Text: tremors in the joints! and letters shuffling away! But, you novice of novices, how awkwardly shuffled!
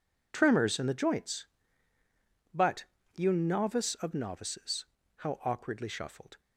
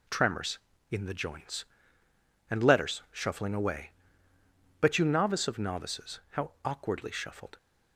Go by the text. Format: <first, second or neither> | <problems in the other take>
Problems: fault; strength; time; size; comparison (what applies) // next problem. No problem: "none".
second | skips "and letters shuffling away"; at 1.9 s